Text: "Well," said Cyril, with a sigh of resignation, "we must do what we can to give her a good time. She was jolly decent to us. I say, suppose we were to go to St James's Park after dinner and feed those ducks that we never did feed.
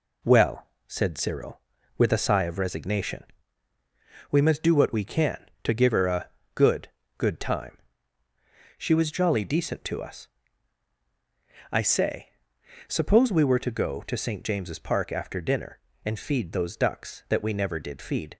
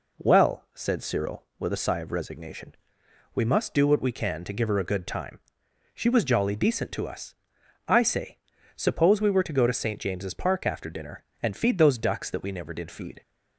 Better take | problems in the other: second | pauses between "a" and "good"; slight; at 6.2 s; 0.26 s long // says "good" twice; at 7.1 s

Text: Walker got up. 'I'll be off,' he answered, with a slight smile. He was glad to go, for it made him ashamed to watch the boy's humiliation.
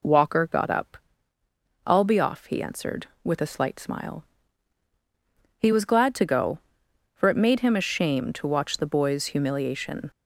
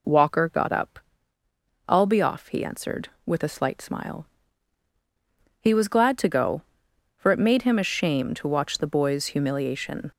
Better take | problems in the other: neither | none

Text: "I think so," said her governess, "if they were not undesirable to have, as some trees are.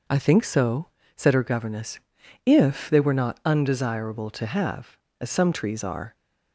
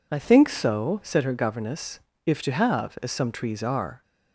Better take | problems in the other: first | skips "they were not undesirable"; at 2.4 s

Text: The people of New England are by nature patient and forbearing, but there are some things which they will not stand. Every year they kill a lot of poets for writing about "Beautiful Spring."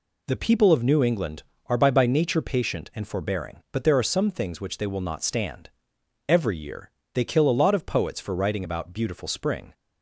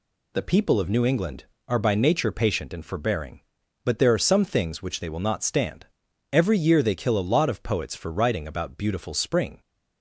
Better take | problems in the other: second | says "by" twice; at 1.9 s // pauses between "year" and "they"; slight; at 6.9 s; 0.22 s long

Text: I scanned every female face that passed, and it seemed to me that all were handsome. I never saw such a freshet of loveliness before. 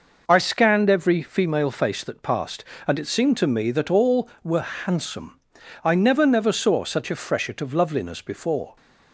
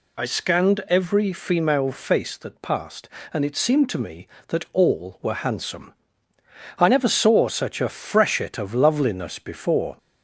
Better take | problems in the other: second | says "never" twice; at 6.2 s

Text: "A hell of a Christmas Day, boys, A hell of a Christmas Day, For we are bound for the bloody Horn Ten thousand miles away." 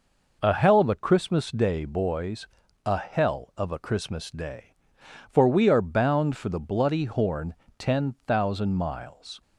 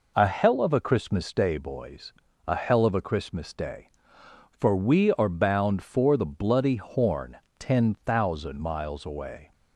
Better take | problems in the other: second | pauses between "Horn" and "Ten"; slight; at 7.5 s; 0.24 s long; slight in the second // stops before "away"; at 9.4 s

